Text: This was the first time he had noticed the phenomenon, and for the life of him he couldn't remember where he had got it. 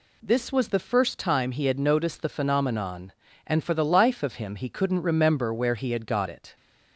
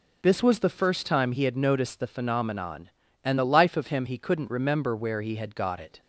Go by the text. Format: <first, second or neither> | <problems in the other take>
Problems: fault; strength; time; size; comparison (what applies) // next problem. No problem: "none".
first | skips "for"; at 3.3 s